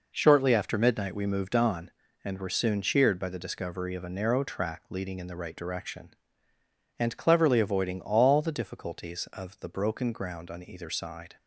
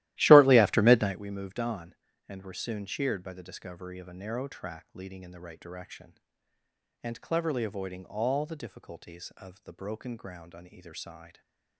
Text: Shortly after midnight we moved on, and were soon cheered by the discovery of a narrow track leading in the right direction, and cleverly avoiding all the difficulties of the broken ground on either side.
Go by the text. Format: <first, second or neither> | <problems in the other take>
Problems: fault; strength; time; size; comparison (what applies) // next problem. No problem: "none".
first | starts louder than the rest; strong; until 1.2 s; 15.5 dB // stays silent after the last word; slight; from 11.2 s on; 0.5 s long